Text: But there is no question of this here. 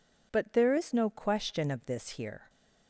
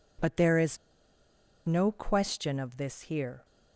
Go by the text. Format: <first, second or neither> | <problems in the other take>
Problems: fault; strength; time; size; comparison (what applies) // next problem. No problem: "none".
first | pauses between "is" and "no"; noticeable; at 0.7 s; 0.89 s long